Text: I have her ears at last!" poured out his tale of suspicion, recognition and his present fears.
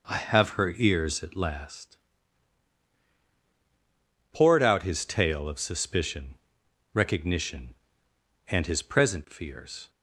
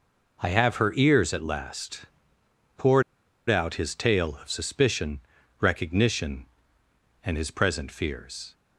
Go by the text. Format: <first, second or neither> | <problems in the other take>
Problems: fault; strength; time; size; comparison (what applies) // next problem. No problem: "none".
first | pauses between "poured" and "out"; noticeable; at 3.0 s; 0.46 s long